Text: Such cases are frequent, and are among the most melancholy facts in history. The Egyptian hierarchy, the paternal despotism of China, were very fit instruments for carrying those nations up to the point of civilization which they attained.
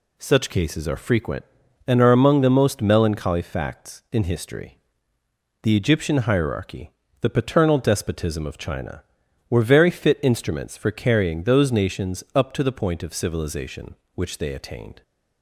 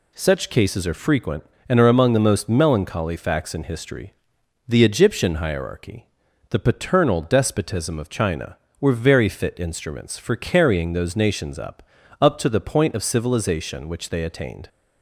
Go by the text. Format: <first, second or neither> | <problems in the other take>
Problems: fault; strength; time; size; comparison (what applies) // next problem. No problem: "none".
first | says "up" twice; at 12.2 s